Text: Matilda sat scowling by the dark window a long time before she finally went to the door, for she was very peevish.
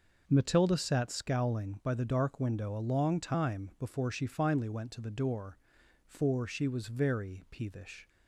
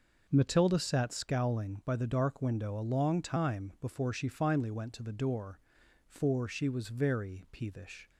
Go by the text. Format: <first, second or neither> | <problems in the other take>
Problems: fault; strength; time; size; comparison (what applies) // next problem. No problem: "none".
neither | none